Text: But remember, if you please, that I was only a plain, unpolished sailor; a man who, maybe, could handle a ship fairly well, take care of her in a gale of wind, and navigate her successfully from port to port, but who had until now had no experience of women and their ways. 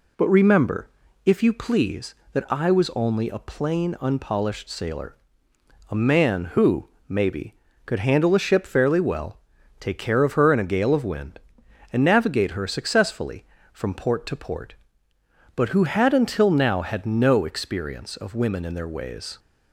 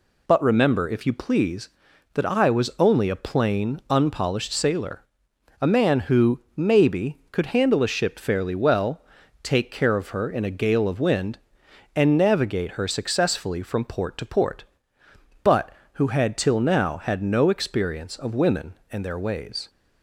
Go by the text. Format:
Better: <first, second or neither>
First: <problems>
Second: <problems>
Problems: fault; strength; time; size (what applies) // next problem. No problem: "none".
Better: first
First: none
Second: says "till" for "until"; at 16.3 s